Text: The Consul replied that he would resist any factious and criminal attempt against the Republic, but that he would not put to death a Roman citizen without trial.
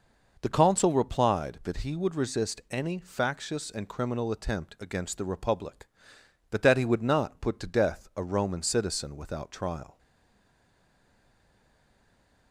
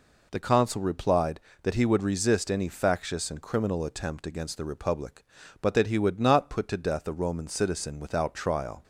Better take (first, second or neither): second